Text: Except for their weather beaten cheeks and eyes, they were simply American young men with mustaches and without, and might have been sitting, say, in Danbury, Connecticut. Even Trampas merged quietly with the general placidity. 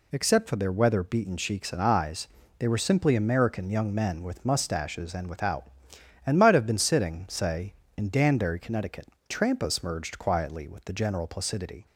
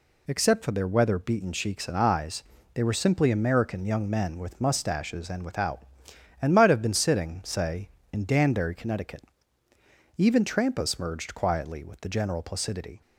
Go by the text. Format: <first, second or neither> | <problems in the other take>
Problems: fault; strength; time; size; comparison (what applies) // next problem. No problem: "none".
second | skips "Even"; at 9.1 s